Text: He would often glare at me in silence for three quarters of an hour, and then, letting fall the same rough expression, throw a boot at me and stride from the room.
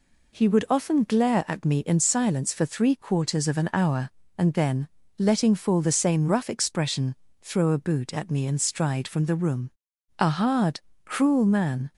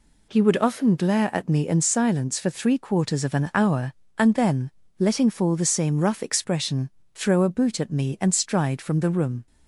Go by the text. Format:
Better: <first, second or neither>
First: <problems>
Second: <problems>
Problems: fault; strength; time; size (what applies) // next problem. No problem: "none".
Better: second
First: goes on to say "A hard cruel man"; strong; from 10.1 s on; 1.7 s long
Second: none